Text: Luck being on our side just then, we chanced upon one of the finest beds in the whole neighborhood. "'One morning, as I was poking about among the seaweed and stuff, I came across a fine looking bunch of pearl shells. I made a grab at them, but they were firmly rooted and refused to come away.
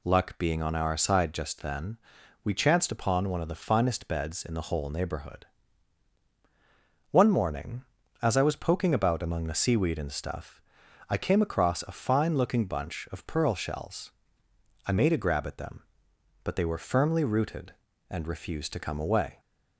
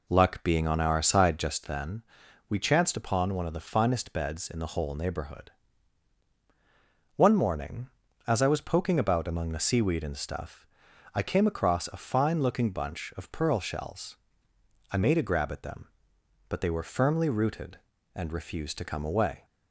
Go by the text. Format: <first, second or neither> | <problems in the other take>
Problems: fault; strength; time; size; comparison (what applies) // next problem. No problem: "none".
first | starts louder than the rest; until 1.8 s; 3.5 dB